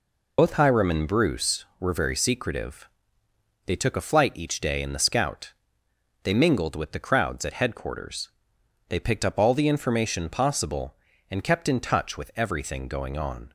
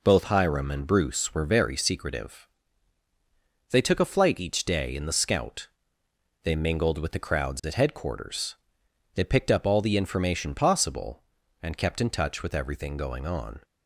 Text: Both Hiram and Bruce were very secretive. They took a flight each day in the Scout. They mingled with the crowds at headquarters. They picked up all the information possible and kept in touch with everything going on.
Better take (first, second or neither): second